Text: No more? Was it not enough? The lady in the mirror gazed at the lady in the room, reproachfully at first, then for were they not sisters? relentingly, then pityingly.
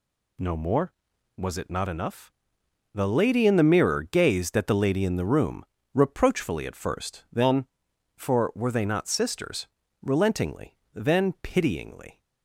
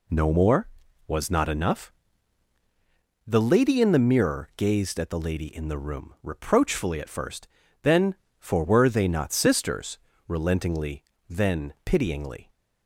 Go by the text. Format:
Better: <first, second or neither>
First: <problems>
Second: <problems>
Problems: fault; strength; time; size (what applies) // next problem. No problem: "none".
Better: first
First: none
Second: skips "it"; at 1.2 s